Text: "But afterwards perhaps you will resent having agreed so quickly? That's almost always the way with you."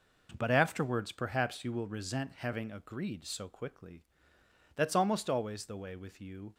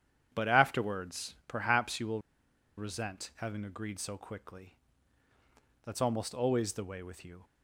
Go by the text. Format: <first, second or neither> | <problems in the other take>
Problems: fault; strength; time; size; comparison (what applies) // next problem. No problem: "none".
first | starts louder than the rest; strong; until 1.3 s; 9 dB // pauses between "will" and "resent"; noticeable; at 2.2 s; 0.57 s long